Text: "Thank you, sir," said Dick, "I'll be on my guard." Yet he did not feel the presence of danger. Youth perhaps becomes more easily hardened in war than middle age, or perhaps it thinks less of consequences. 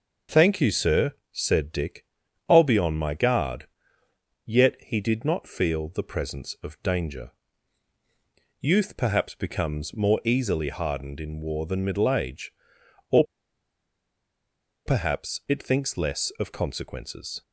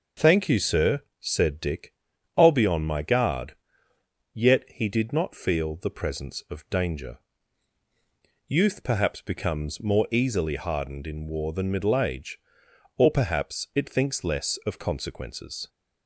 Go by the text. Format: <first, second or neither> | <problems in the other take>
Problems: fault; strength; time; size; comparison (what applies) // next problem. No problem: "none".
second | pauses between "or" and "perhaps"; strong; at 13.2 s; 1.6 s long